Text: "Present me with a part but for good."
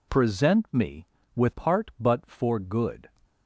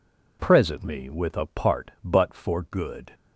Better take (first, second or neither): second